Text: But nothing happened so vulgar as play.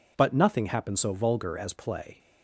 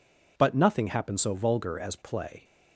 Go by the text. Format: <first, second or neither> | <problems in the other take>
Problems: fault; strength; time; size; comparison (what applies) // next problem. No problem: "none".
neither | none